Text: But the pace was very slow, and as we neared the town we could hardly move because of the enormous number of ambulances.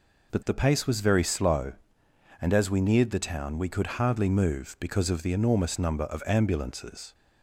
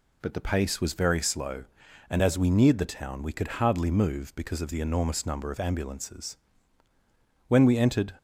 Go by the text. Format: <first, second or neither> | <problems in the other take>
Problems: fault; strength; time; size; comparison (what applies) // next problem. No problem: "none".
first | goes on to say "When we entered"; noticeable; from 7.4 s on; 0.66 s long